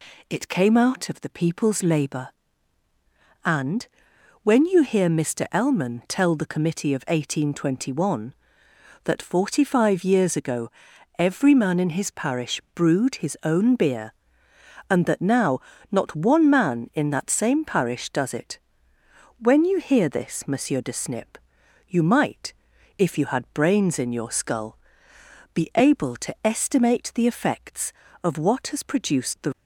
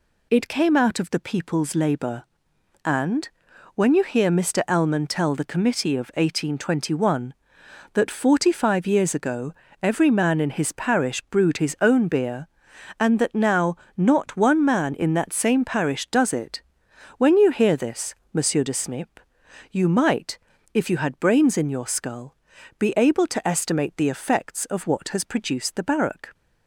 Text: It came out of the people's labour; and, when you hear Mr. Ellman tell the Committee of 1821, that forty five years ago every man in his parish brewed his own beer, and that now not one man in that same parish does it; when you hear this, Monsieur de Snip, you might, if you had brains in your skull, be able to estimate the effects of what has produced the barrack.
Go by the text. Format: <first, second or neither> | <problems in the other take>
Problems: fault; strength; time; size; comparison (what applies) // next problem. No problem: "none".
second | pauses between "ago" and "every"; noticeable; at 10.6 s; 0.48 s long; slight in the second // pauses between "now" and "not"; slight; at 15.5 s; 0.32 s long; slight in the second // stops before "barrack"; at 29.5 s